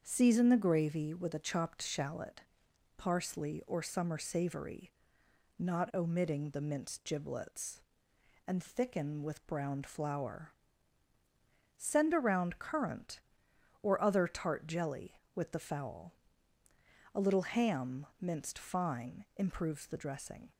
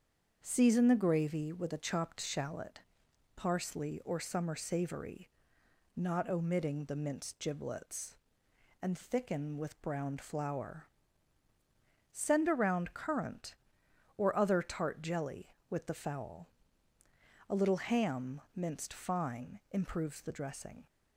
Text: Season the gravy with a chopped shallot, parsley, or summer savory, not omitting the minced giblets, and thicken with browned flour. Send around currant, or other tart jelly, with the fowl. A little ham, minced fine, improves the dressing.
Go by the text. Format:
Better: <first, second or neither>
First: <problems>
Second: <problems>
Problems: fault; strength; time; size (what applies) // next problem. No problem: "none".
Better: neither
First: starts louder than the rest; until 1.0 s; 7 dB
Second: starts louder than the rest; until 1.4 s; 7 dB